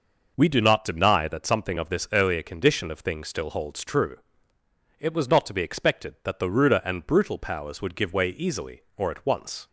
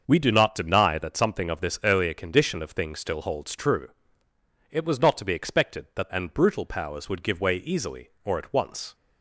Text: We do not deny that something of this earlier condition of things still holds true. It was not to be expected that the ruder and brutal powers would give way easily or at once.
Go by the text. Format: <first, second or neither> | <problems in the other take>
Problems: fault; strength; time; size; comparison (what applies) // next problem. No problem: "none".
first | starts louder than the rest; until 1.0 s; 6.5 dB // skips "the ruder"; at 6.1 s